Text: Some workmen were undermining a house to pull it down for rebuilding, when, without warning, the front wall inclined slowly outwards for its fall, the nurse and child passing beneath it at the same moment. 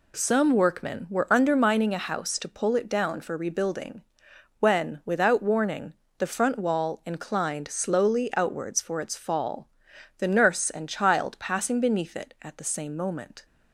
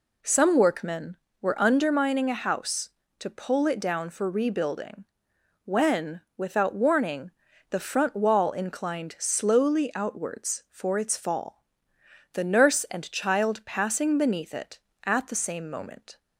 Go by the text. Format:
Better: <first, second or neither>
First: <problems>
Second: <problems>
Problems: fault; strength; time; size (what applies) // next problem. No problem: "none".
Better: neither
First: none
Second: none